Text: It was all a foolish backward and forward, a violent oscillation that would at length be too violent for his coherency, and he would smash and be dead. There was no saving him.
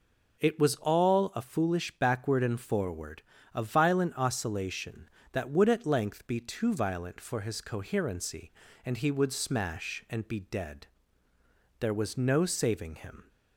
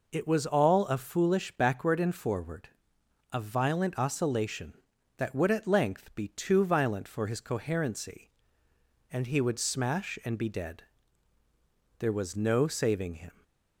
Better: neither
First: none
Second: none

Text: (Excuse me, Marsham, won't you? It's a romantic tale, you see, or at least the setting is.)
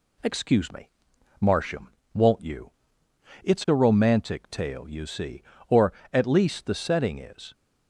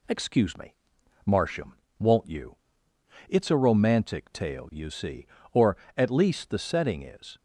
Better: neither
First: none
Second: none

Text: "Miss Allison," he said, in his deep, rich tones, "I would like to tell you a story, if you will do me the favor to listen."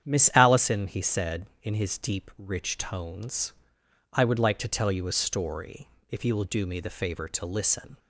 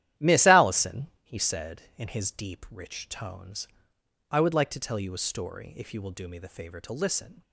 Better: first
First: starts louder than the rest; strong; until 1.0 s; 9 dB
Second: gets quieter; strong; throughout; 9 dB // starts louder than the rest; strong; until 1.3 s; 12.5 dB

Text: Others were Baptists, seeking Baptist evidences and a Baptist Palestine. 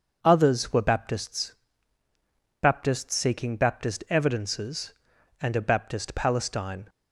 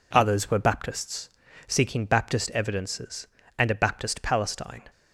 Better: second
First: starts louder than the rest; until 1.2 s; 6.5 dB // says "Baptists" twice; at 2.6 s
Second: none

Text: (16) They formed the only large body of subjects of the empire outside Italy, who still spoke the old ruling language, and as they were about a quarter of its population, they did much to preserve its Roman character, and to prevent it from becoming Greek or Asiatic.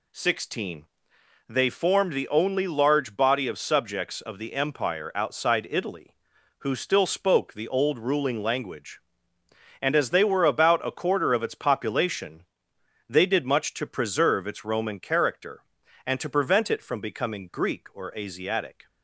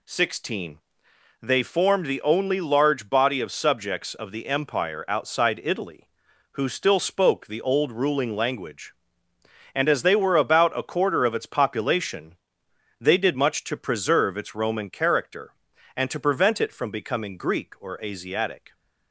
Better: neither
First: none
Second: none

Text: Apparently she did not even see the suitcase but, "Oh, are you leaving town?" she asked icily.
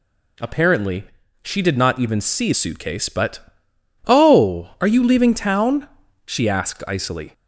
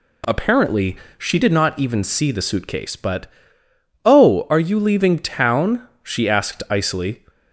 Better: second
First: pauses between "Apparently" and "she"; at 1.0 s; 0.40 s long // skips "the"; at 2.5 s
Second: pauses between "Apparently" and "she"; slight; at 0.9 s; 0.20 s long

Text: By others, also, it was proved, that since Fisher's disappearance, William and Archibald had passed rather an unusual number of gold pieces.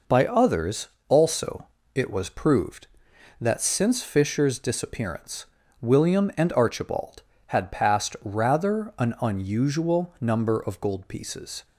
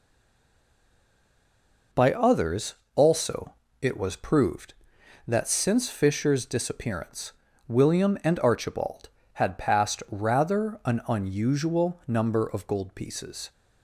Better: first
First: none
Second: stays silent before the first word; noticeable; until 1.9 s; 1.9 s long

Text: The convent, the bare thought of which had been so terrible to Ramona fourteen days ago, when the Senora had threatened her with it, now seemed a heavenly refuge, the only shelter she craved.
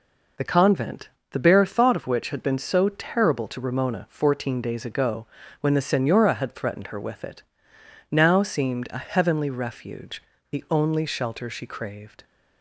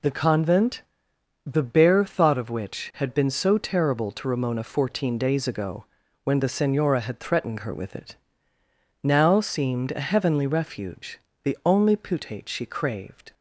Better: first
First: none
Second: says "putate" for "shelter"; at 11.9 s

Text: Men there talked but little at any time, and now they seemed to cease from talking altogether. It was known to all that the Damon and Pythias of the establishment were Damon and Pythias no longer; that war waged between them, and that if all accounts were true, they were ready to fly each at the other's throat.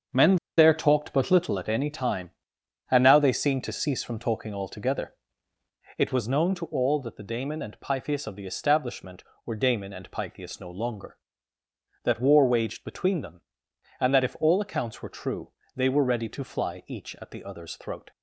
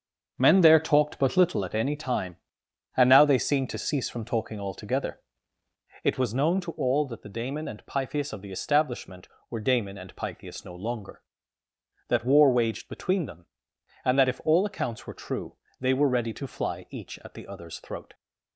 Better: second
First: starts louder than the rest; until 1.3 s; 7 dB // pauses between "Men" and "there"; slight; at 0.3 s; 0.22 s long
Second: starts louder than the rest; until 1.3 s; 7 dB

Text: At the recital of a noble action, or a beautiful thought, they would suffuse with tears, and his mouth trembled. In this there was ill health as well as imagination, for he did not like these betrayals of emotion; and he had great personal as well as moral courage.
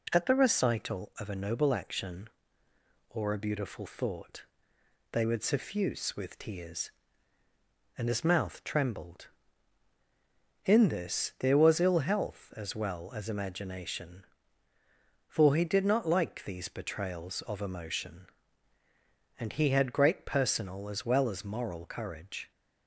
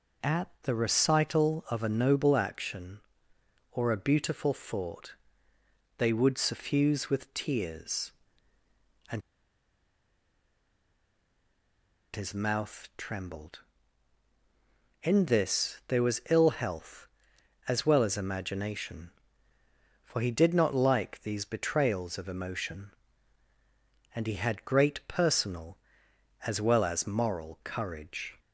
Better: first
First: none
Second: pauses between "and" and "his"; strong; at 9.2 s; 2.9 s long

